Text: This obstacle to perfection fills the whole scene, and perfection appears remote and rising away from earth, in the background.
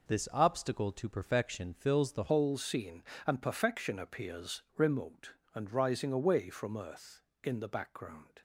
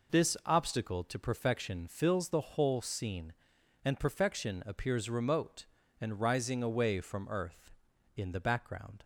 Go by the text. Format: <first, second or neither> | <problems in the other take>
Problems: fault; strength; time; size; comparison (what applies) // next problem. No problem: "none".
second | changes voice at "whole"; from 2.3 s on; 6.1 s long // pauses between "appears" and "remote"; slight; at 4.6 s; 0.16 s long